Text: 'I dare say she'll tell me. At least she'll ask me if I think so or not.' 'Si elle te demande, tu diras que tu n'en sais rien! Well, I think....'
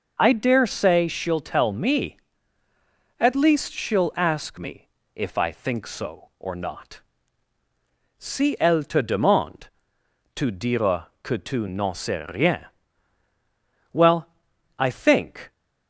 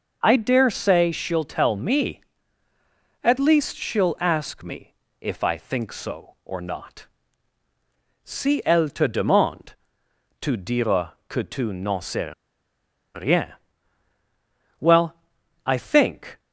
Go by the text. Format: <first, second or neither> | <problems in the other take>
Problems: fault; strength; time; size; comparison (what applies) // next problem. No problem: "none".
first | pauses between "me" and "if"; slight; at 4.9 s; 0.26 s long; slight in the first // pauses between "diras" and "que"; slight; at 11.1 s; 0.16 s long; slight in the first // pauses between "sais" and "rien"; noticeable; at 12.3 s; 0.84 s long